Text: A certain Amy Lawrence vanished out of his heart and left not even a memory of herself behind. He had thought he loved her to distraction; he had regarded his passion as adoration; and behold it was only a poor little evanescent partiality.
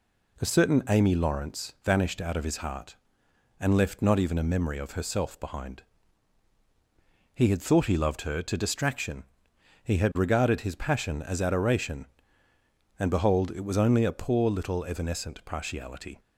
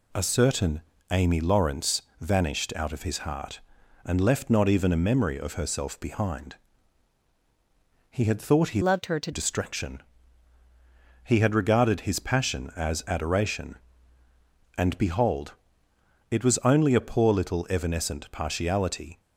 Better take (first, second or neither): first